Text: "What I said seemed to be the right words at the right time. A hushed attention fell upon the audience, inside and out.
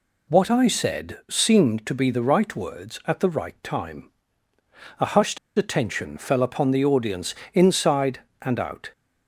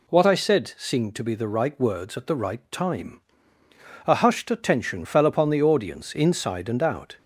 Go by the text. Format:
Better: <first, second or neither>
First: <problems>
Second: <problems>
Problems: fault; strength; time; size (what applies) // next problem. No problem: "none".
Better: second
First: pauses between "hushed" and "attention"; slight; at 5.3 s; 0.19 s long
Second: none